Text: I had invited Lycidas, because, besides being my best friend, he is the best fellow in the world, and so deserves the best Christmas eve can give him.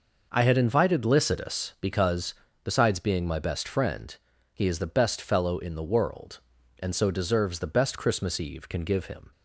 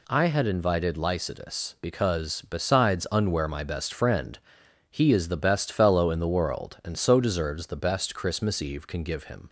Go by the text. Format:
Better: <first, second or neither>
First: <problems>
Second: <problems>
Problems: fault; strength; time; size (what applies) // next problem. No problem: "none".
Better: first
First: none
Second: says "unwear" for "being"; at 3.1 s